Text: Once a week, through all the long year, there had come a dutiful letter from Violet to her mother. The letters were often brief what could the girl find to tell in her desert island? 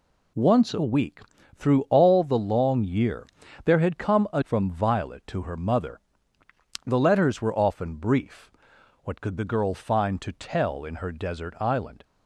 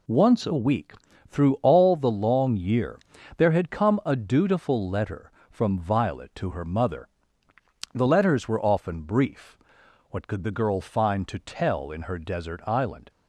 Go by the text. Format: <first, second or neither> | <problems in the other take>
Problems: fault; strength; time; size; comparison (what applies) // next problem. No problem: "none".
second | skips "dutiful letter"; at 4.4 s // pauses between "brief" and "what"; noticeable; at 8.5 s; 0.54 s long; noticeable in the second